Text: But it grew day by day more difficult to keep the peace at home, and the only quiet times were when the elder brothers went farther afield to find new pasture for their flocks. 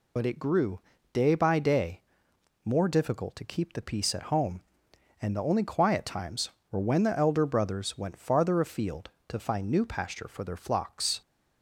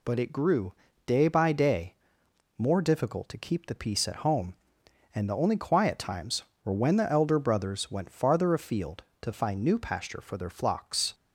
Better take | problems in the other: second | loses the start of "But"; at 0.1 s; 55 ms // pauses between "grew" and "day"; slight; at 0.7 s; 0.32 s long; slight in the second // pauses between "day" and "more"; noticeable; at 2.0 s; 0.62 s long; noticeable in the second

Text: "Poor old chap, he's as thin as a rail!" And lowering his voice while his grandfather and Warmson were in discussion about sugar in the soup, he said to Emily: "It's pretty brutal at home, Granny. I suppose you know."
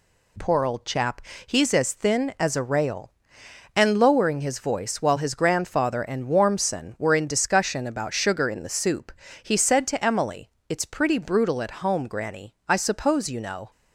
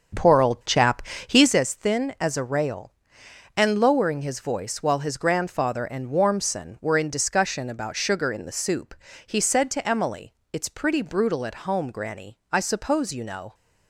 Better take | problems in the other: first | starts louder than the rest; strong; until 1.6 s; 7 dB

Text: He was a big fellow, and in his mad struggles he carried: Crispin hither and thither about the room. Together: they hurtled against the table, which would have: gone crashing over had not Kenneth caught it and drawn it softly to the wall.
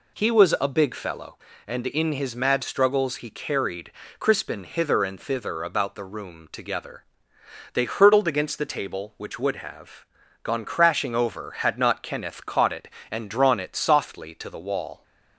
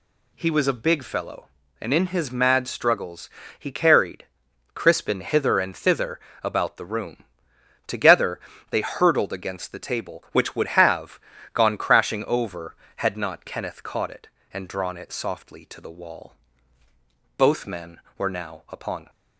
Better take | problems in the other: first | pauses between "struggles" and "he"; slight; at 3.2 s; 0.30 s long // pauses between "thither" and "about"; slight; at 6.1 s; 0.22 s long // goes on to say "Both men were now upon"; strong; from 17.3 s on; 1.7 s long

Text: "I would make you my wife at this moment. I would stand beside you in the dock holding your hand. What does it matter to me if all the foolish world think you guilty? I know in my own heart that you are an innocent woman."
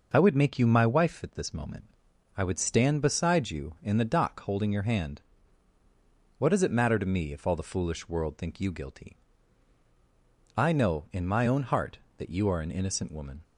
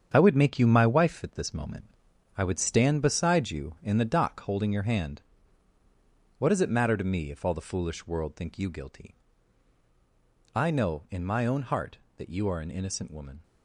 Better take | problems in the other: first | gets quieter; strong; throughout; 8.5 dB

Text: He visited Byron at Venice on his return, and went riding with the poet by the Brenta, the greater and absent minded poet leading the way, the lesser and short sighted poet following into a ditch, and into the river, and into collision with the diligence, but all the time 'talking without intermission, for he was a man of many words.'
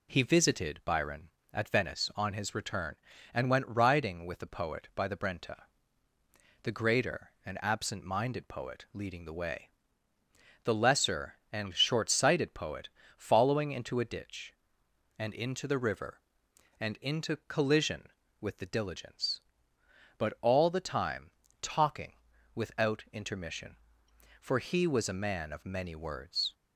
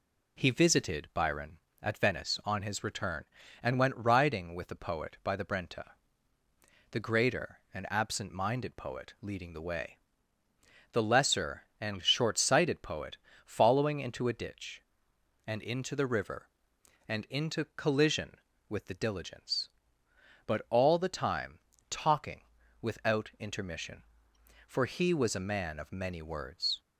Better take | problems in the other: neither | pauses between "poet" and "following"; slight; the same in both // pauses between "time" and "talking"; slight; the same in both // pauses between "talking" and "without"; the same in both

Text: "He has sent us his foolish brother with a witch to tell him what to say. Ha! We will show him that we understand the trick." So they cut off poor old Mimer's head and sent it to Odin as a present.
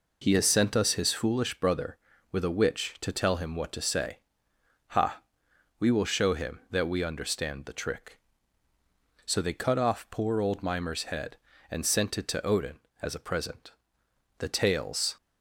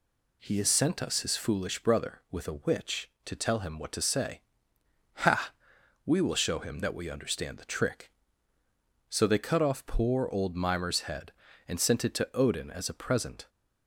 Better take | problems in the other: second | goes on to say "The tales"; noticeable; from 14.3 s on; 0.78 s long

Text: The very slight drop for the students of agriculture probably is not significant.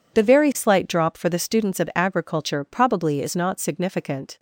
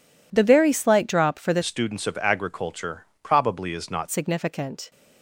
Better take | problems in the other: first | changes voice from "students" to "not"; from 1.6 to 4.0 s; 2.4 s long // pauses between "agriculture" and "probably"; slight; at 3.0 s; 0.16 s long

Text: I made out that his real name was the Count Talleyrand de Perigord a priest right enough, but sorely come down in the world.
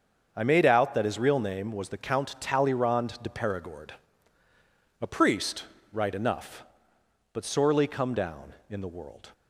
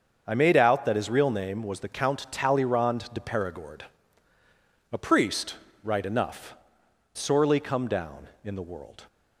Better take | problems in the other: first | starts louder than the rest; until 1.2 s; 6.5 dB; also in the first // pauses between "Perigord" and "a"; at 3.8 s; 1.1 s long; also in the first // pauses between "priest" and "right"; slight; at 5.5 s; 0.28 s long; slight in the first // skips "but"; at 6.8 s

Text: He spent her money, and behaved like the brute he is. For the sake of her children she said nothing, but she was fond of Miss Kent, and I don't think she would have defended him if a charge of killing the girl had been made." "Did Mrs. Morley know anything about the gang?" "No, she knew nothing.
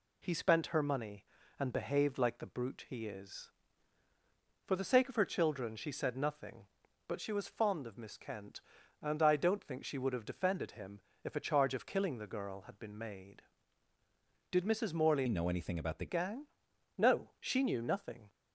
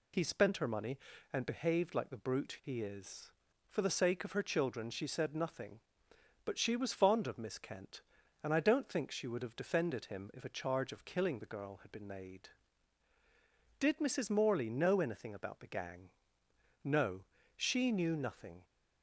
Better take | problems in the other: second | pauses between "him" and "if"; slight; at 11.0 s; 0.24 s long // changes voice from "know" to "the"; from 15.2 to 16.0 s; 0.8 s long

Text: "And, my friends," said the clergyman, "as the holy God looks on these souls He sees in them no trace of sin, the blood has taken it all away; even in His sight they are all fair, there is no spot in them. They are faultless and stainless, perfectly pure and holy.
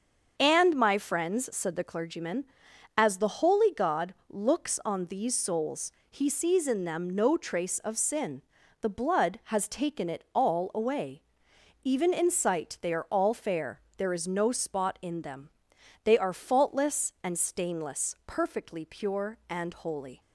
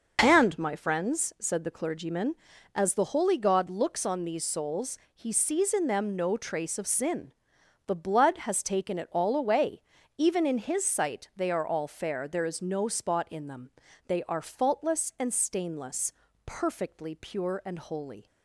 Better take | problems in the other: second | starts louder than the rest; until 1.3 s; 7 dB // pauses between "souls" and "He"; slight; at 5.9 s; 0.18 s long; slight in the second // skips "His"; at 12.3 s

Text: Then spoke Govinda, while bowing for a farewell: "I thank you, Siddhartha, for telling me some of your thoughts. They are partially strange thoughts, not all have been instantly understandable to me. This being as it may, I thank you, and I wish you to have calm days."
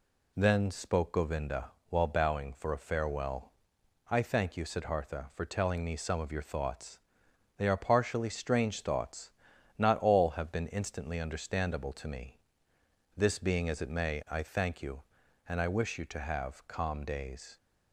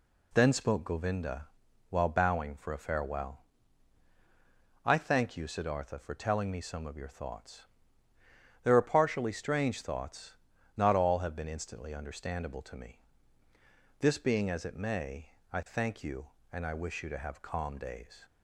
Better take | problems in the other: first | says "There" for "They"; at 8.6 s

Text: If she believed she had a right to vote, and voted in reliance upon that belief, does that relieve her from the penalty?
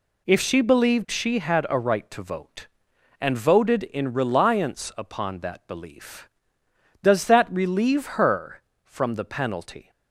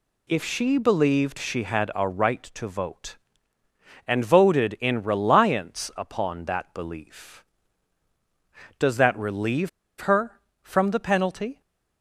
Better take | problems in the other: first | pauses between "relieve" and "her"; slight; at 9.6 s; 0.30 s long

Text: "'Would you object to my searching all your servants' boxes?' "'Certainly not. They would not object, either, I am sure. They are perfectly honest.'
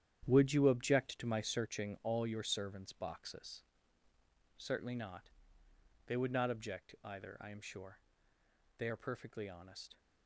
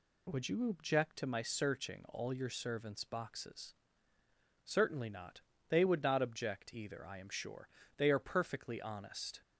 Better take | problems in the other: second | gets quieter; strong; throughout; 10 dB

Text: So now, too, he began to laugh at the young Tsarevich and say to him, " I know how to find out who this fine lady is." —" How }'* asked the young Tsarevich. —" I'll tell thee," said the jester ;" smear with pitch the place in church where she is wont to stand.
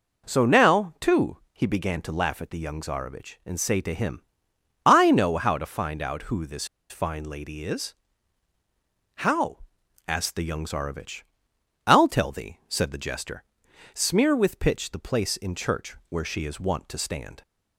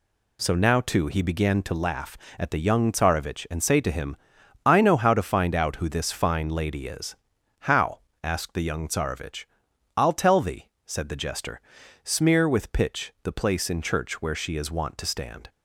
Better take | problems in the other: second | pauses between "this" and "fine"; slight; at 6.6 s; 0.24 s long

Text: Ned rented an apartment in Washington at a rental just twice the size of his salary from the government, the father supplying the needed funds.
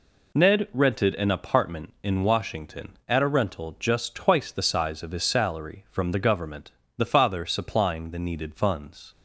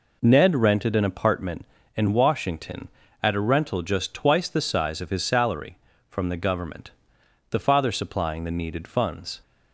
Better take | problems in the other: neither | none

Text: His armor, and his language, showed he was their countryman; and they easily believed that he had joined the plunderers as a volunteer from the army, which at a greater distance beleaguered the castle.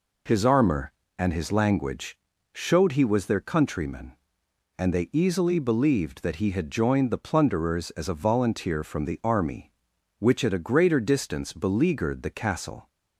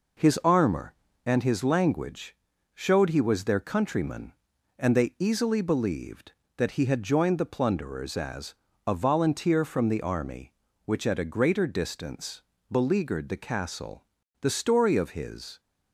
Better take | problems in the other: first | pauses between "as" and "a"; slight; at 8.5 s; 0.28 s long // pauses between "distance" and "beleaguered"; slight; at 12.4 s; 0.28 s long // goes on to say "The story of his"; noticeable; from 14.3 s on; 1.2 s long

